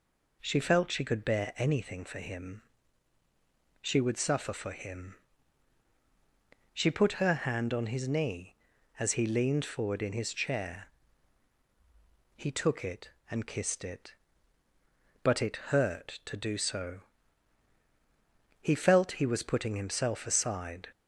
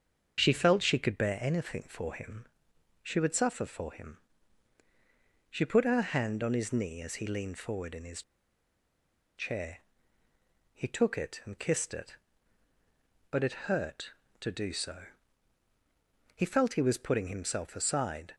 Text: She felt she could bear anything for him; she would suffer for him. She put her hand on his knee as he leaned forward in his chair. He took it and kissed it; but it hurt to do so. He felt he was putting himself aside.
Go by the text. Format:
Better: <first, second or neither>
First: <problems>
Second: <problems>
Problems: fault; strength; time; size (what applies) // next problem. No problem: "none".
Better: first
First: none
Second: starts louder than the rest; until 1.4 s; 7 dB // pauses between "his" and "chair"; at 8.2 s; 1.1 s long